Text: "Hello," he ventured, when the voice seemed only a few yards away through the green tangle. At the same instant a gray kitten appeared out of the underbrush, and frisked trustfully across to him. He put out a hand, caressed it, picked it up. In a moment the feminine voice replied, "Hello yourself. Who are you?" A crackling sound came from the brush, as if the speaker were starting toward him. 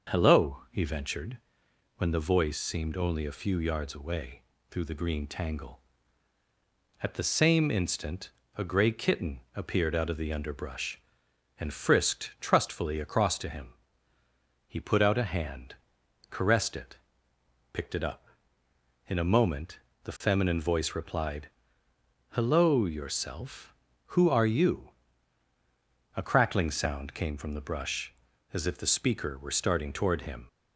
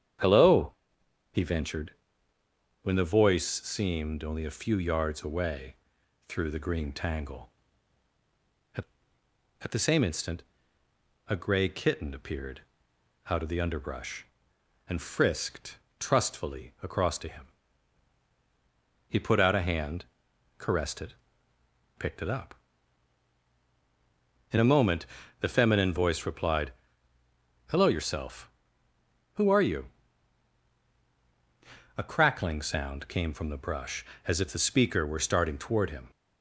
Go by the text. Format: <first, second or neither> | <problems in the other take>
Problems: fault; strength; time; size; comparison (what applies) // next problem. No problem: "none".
first | starts louder than the rest; strong; until 1.7 s; 8.5 dB; noticeable in the first // pauses between "away" and "through"; noticeable; at 5.7 s; 0.52 s long; slight in the first // says "At" twice; at 9.6 s // pauses between "instant" and "a"; noticeable; at 10.4 s; 0.86 s long; slight in the first // pauses between "appeared" and "out"; noticeable; at 12.5 s; 0.70 s long // pauses between "frisked" and "trustfully"; slight; at 15.7 s; 0.22 s long // pauses between "moment" and "the"; slight; at 25.0 s; 0.32 s long; slight in the first